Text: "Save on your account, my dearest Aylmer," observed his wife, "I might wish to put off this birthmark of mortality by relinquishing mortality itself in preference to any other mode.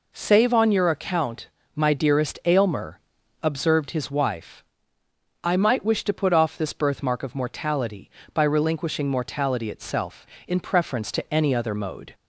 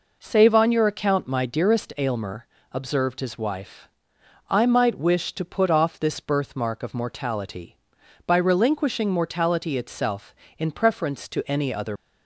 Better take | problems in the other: first | stops before "mode"; at 11.9 s

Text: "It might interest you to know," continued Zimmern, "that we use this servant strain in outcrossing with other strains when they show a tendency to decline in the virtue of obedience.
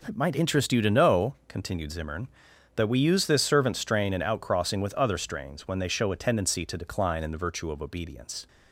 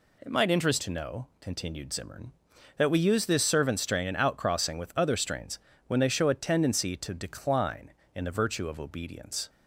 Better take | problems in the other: first | skips "you"; at 0.8 s // pauses between "strains" and "when"; slight; at 5.5 s; 0.28 s long

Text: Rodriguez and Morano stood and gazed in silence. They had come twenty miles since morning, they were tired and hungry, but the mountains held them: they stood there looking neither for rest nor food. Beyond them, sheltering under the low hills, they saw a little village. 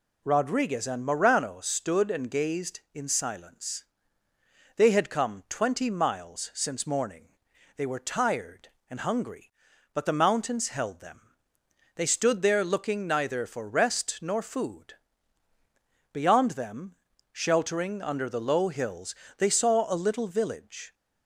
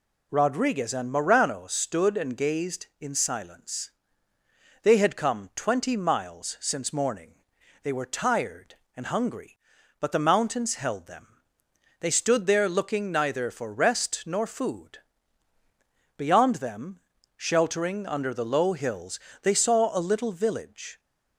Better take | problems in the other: neither | none

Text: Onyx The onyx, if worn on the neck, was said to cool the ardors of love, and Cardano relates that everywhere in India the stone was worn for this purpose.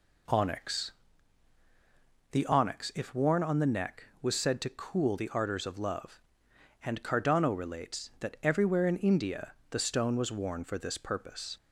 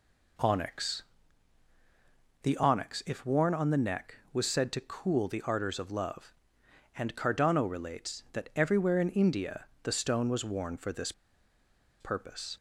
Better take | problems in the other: first | pauses between "Onyx" and "The"; strong; at 1.0 s; 1.4 s long; strong in the first // pauses between "India" and "the"; slight; at 9.6 s; 0.18 s long; slight in the first // pauses between "this" and "purpose"; noticeable; at 11.1 s; 0.87 s long

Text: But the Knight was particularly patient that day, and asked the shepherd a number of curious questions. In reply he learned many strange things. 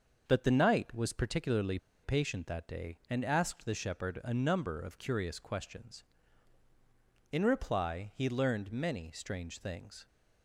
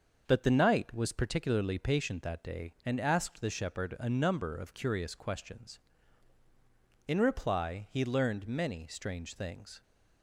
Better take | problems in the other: second | starts louder than the rest; until 1.2 s; 6.5 dB; also in the second // pauses between "particularly" and "patient"; slight; at 1.7 s; 0.26 s long

